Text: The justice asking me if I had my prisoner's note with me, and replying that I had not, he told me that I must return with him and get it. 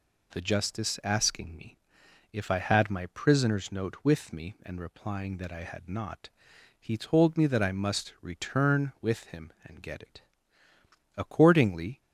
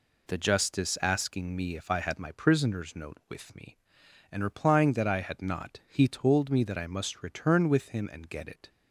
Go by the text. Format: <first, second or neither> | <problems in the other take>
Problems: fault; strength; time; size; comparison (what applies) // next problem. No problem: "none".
second | pauses between "me" and "if"; noticeable; at 1.7 s; 0.56 s long // goes on to say "Accordingly"; noticeable; from 11.1 s on; 0.84 s long